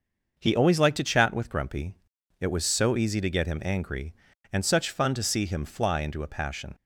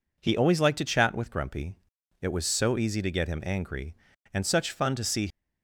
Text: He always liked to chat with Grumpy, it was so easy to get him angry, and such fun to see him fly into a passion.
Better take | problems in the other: first | stops before "him fly into a passion"; at 5.2 s

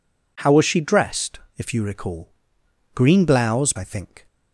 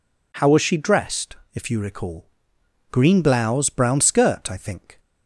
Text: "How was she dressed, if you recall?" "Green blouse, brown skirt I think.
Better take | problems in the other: second | skips "brown skirt"; at 3.7 s

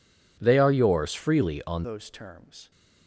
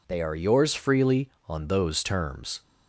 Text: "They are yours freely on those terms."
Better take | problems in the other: second | changes voice at "those"; from 1.8 s on; 0.9 s long

